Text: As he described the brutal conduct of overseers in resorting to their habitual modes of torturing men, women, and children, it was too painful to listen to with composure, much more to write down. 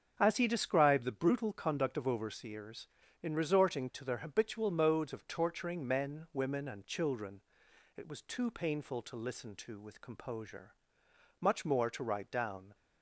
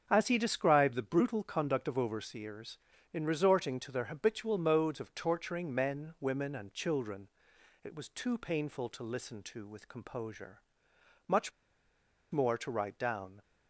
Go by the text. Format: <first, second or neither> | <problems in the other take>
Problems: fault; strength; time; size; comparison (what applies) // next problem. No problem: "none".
first | starts louder than the rest; until 1.1 s; 7 dB; also in the first // pauses between "much" and "more"; noticeable; at 11.5 s; 0.80 s long